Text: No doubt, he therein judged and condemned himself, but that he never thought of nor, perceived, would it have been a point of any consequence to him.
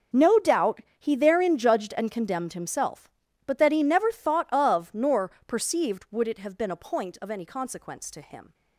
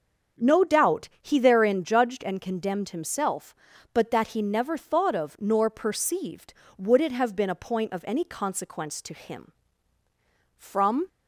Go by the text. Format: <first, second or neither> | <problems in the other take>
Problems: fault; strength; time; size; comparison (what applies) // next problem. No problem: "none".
first | starts louder than the rest; until 1.5 s; 6.5 dB; also in the first // goes on to say "From"; from 10.5 s on; 0.50 s long